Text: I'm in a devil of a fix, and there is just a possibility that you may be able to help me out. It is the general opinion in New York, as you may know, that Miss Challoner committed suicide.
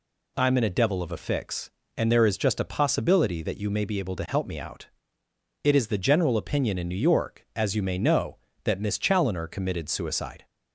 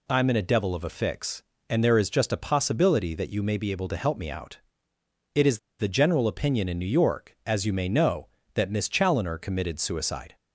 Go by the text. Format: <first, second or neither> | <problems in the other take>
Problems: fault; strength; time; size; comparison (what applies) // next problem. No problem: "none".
first | pauses between "is" and "the"; slight; at 5.5 s; 0.20 s long